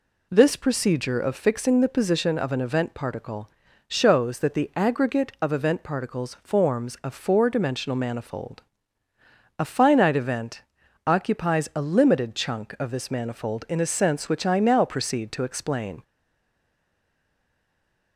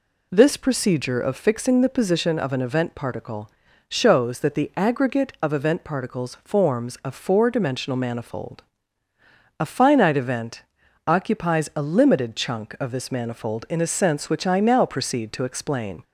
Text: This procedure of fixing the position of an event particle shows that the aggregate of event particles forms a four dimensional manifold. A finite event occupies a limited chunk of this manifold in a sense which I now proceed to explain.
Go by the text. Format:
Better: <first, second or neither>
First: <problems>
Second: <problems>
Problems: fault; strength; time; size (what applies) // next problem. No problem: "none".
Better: second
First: pauses between "particle" and "shows"; at 3.4 s; 0.38 s long // pauses between "event" and "occupies"; noticeable; at 10.6 s; 0.46 s long // stays silent after the last word; from 16.0 s on; 2.1 s long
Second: pauses between "particle" and "shows"; at 3.4 s; 0.38 s long // pauses between "event" and "occupies"; noticeable; at 10.6 s; 0.46 s long